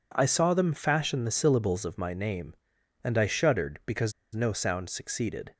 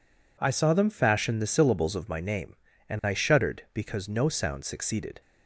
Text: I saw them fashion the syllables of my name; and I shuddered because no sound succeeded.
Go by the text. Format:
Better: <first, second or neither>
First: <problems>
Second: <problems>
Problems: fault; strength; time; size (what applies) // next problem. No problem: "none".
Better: second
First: pauses between "because" and "no"; slight; at 4.1 s; 0.22 s long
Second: none